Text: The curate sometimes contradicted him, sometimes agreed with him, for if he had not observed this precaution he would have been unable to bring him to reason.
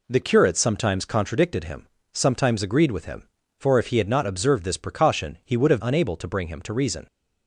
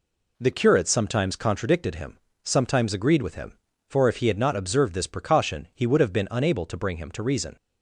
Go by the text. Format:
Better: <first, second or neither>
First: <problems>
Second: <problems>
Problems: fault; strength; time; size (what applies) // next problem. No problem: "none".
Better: second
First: skips "been"; at 5.8 s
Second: none